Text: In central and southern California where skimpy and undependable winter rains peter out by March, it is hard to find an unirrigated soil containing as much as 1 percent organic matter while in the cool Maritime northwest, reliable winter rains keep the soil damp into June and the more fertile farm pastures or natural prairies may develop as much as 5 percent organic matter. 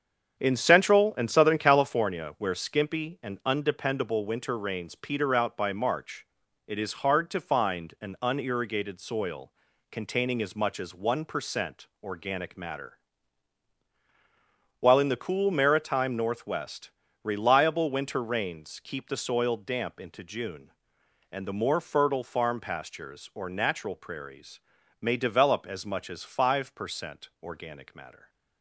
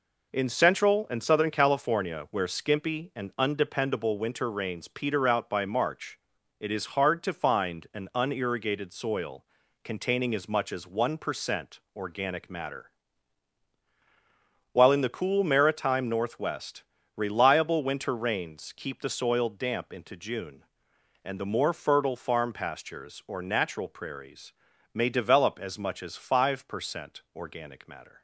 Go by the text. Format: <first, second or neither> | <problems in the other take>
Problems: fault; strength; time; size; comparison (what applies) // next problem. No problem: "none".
second | starts louder than the rest; strong; until 2.0 s; 7.5 dB // pauses between "soil" and "containing"; at 9.5 s; 0.38 s long; also in the second // pauses between "percent" and "organic"; slight; at 11.8 s; 0.16 s long; slight in the second // pauses between "matter" and "while"; strong; at 12.9 s; 1.8 s long; strong in the second // pauses between "prairies" and "may"; at 24.5 s; 0.42 s long; also in the second